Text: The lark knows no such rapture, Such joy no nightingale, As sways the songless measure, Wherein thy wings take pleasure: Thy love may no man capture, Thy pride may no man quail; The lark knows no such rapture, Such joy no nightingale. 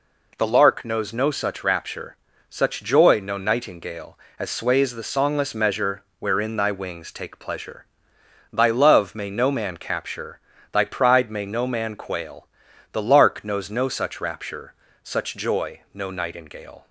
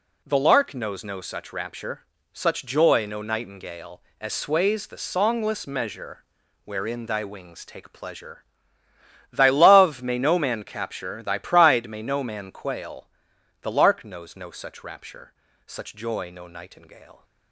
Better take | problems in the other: neither | none

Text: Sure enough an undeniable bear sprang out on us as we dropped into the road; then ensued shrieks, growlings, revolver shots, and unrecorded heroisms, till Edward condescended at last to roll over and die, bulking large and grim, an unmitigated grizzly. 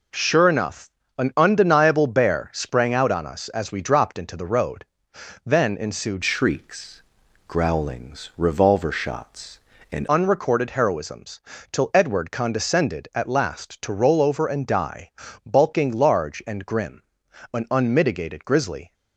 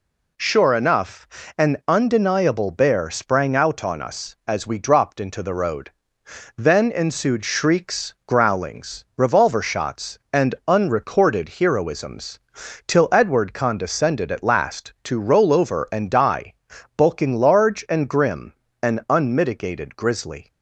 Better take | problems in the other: second | pauses between "enough" and "an"; slight; at 0.9 s; 0.28 s long; slight in the second // changes voice from "shrieks" to "and"; from 6.2 to 10.0 s; 3.8 s long

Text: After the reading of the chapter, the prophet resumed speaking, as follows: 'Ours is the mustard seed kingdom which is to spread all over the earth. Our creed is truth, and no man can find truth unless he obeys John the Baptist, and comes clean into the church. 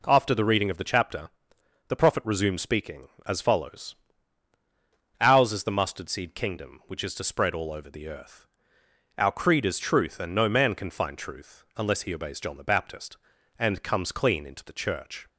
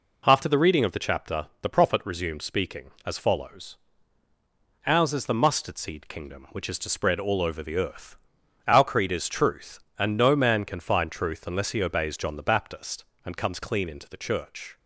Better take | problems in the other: neither | none

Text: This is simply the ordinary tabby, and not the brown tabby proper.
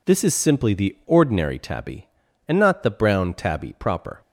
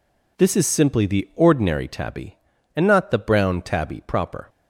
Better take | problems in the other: neither | none

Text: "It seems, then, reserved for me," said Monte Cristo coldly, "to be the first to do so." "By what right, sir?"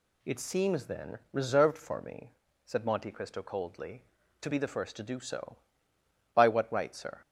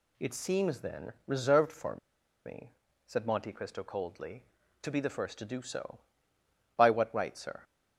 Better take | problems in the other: first | pauses between "for" and "me"; noticeable; at 1.9 s; 0.48 s long

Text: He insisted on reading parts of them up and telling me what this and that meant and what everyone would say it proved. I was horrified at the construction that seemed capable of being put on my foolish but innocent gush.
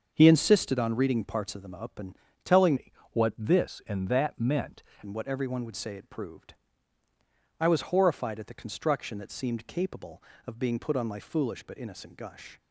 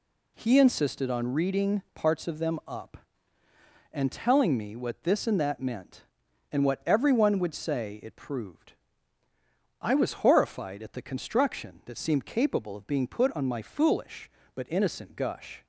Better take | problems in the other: second | starts louder than the rest; until 1.1 s; 6.5 dB // pauses between "and" and "telling"; slight; at 2.1 s; 0.28 s long // changes voice from "me" to "meant"; from 2.7 to 4.8 s; 2.1 s long // pauses between "me" and "what"; slight; at 2.9 s; 0.22 s long

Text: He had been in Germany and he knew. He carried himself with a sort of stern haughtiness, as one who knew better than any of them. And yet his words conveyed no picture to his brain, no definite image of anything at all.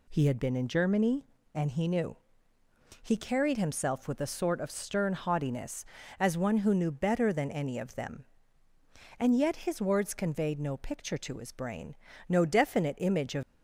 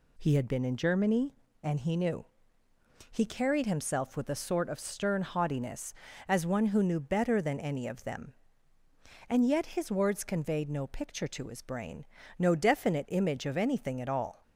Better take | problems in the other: second | stops before "anything at all"; at 13.4 s

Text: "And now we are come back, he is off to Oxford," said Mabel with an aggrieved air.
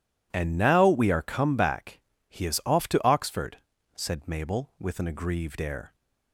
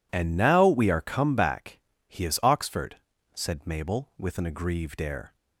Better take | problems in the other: first | skips "off to"; at 2.4 s

